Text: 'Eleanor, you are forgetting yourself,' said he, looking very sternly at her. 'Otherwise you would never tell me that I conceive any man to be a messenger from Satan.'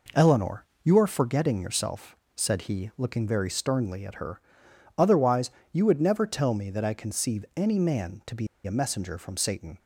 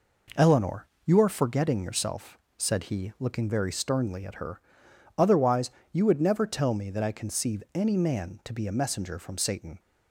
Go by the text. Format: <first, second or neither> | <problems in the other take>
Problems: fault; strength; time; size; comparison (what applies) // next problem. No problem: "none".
second | pauses between "Otherwise" and "you"; slight; at 5.5 s; 0.22 s long; slight in the second // pauses between "be" and "a"; slight; at 8.4 s; 0.19 s long